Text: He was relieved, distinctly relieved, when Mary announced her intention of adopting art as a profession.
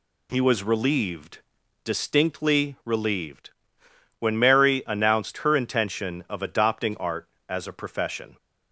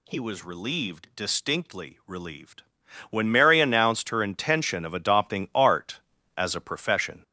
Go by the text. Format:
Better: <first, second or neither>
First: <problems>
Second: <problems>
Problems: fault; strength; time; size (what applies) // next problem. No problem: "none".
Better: first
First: none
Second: gets louder; noticeable; throughout; 5.5 dB